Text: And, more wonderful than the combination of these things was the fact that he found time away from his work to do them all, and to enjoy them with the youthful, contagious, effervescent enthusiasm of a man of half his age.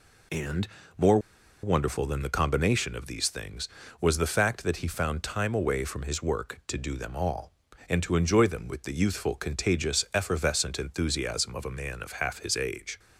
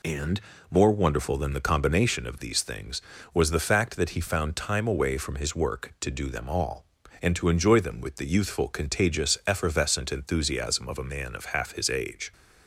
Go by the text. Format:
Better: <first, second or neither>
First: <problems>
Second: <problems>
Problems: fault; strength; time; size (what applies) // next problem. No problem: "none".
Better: second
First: pauses between "more" and "wonderful"; at 1.1 s; 0.44 s long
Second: none